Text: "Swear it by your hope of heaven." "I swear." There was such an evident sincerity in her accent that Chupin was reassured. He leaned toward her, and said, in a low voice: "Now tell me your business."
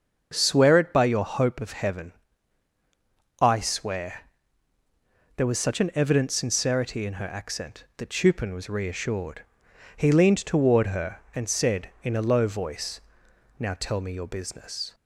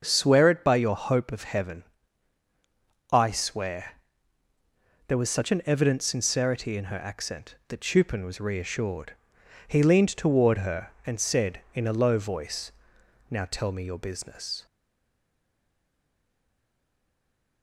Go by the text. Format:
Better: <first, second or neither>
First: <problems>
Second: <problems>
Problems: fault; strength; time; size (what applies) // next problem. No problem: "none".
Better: first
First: starts louder than the rest; until 1.3 s; 6.5 dB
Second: starts louder than the rest; until 1.0 s; 6.5 dB // stays silent after the last word; strong; from 14.6 s on; 3.0 s long